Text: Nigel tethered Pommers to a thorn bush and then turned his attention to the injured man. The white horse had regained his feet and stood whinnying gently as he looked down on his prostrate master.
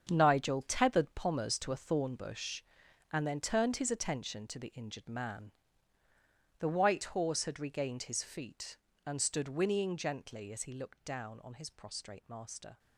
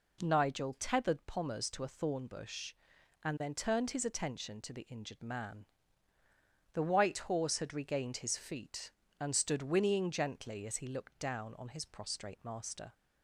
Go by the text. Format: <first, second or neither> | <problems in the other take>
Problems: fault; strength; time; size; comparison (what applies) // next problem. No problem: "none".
second | gets quieter; strong; throughout; 11.5 dB